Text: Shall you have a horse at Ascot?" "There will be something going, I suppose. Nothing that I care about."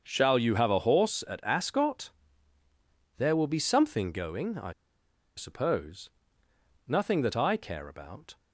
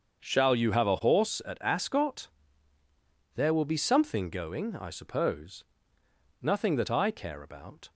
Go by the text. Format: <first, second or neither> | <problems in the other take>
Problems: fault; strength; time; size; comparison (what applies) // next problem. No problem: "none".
second | starts louder than the rest; until 1.0 s; 7 dB; also in the second // pauses between "I" and "suppose"; noticeable; at 4.7 s; 0.64 s long